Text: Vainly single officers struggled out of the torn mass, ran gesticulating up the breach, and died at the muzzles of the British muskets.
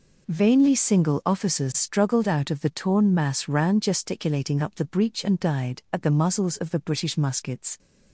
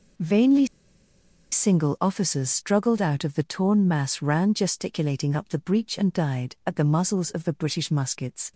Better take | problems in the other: first | pauses between "Vainly" and "single"; noticeable; at 0.6 s; 0.86 s long

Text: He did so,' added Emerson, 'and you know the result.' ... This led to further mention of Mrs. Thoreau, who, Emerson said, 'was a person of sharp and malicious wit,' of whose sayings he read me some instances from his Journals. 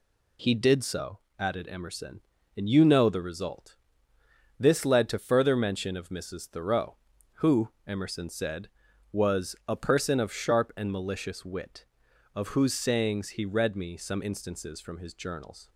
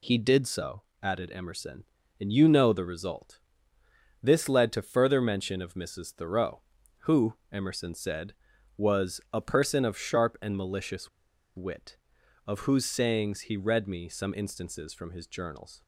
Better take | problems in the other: first | pauses between "malicious" and "wit"; noticeable; at 11.0 s; 0.47 s long

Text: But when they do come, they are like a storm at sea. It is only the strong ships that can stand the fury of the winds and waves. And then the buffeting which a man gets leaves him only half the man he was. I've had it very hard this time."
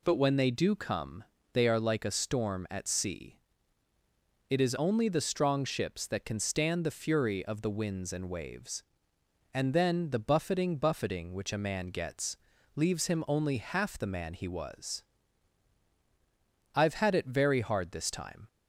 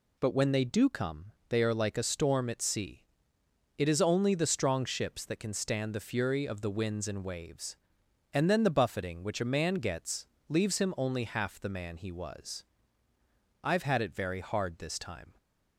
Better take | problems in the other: second | says "buffeting" twice; at 10.7 s // pauses between "gets" and "leaves"; at 12.3 s; 0.38 s long; slight in the second

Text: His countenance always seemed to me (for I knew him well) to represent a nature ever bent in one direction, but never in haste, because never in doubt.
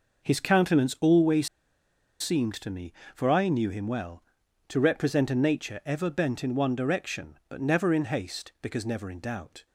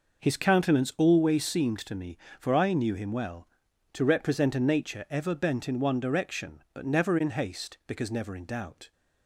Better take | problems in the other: second | pauses between "always" and "seemed"; noticeable; at 1.4 s; 0.73 s long

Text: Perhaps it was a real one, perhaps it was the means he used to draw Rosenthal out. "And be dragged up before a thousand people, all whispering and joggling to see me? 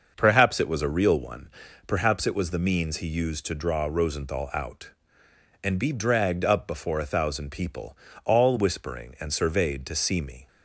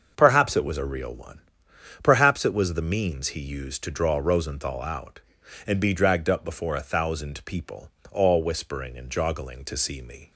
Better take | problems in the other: second | starts louder than the rest; noticeable; until 1.1 s; 6 dB; also in the second // says "surveyed" for "joggling"; at 9.3 s

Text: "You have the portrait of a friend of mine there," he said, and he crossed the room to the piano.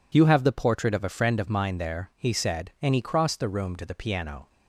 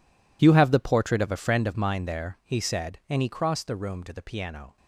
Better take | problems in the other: first | gets quieter; strong; throughout; 16 dB

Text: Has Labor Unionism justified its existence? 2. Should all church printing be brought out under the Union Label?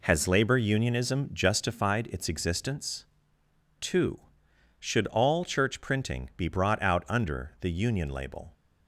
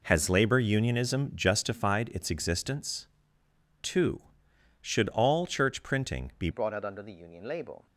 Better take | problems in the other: first | changes voice at "brought"; from 6.5 s on; 1.3 s long

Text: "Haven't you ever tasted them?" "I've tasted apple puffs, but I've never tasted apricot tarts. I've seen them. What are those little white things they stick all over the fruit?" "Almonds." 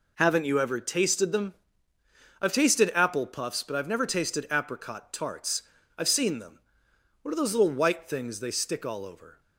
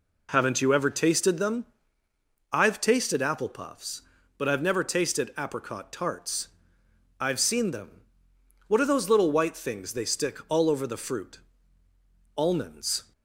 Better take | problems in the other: second | stops before "the fruit Almonds"; at 9.3 s

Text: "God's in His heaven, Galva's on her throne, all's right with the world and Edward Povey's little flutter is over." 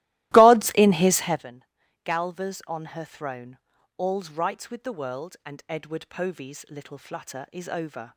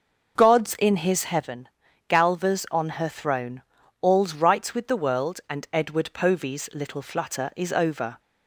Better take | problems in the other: second | starts louder than the rest; strong; until 1.5 s; 17 dB

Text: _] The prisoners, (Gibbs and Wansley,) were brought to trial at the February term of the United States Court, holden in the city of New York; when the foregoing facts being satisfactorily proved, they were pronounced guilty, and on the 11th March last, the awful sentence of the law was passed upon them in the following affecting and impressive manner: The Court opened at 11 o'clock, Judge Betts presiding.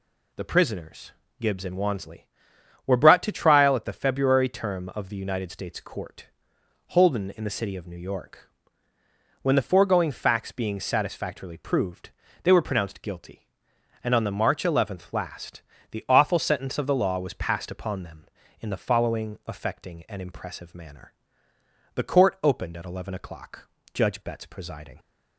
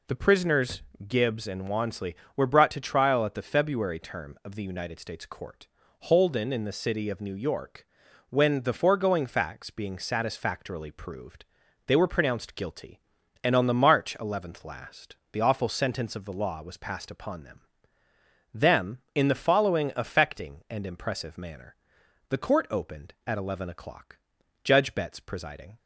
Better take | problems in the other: first | says "them" twice; at 18.5 s

